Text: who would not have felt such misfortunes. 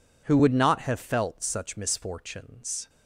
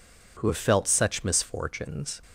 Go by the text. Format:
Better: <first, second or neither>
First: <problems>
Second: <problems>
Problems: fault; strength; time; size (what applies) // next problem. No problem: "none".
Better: first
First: none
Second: skips "would not"; at 0.4 s